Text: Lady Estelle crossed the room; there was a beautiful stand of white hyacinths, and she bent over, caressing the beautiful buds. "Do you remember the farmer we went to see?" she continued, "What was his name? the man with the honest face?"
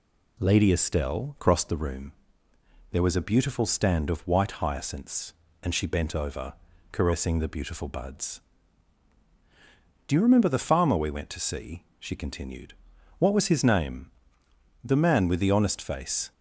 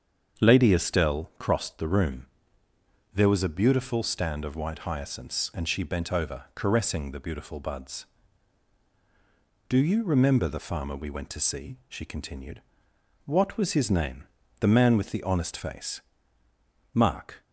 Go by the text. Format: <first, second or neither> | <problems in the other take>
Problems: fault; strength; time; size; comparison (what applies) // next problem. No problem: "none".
first | starts louder than the rest; strong; until 1.4 s; 7 dB // goes on to say "Mark"; from 16.9 s on; 0.50 s long